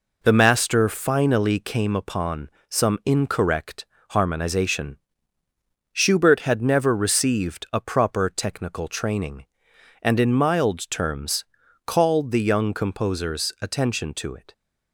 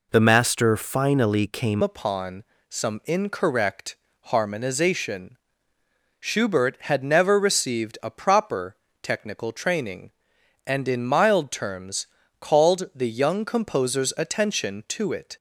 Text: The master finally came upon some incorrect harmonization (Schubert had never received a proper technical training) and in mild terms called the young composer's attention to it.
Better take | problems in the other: first | changes voice at "upon"; from 1.8 s on; 13.5 s long // pauses between "upon" and "some"; slight; at 2.4 s; 0.28 s long; slight in the first // pauses between "incorrect" and "harmonization"; slight; at 3.9 s; 0.24 s long; slight in the first // pauses between "proper" and "technical"; slight; at 8.7 s; 0.26 s long // pauses between "terms" and "called"; slight; at 12.0 s; 0.32 s long; also in the first

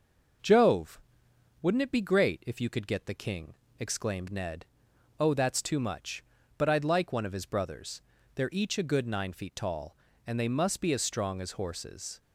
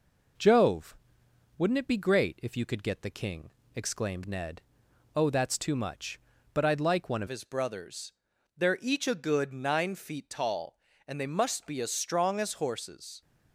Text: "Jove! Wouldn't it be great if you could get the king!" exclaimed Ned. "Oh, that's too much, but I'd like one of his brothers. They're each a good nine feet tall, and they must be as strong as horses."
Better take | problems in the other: first | changes voice at "his"; from 7.2 s on; 6.0 s long

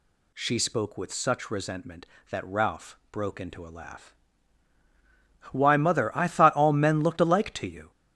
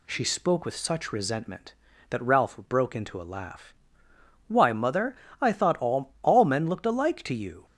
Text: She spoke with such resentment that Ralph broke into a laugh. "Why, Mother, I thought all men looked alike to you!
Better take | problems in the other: first | says "all" twice; at 6.2 s

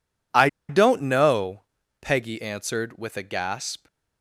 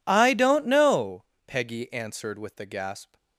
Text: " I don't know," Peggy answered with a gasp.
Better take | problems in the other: second | pauses between "I" and "don't"; slight; at 0.4 s; 0.21 s long

